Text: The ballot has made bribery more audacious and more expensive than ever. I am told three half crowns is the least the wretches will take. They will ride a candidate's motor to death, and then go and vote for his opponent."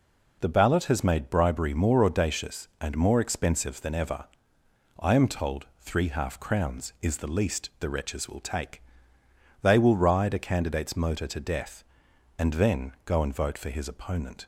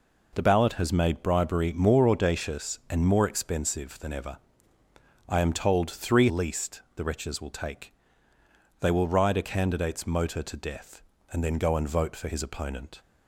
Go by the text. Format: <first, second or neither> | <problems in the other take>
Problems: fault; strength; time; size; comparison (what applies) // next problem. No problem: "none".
first | skips "half crowns is the"; at 6.2 s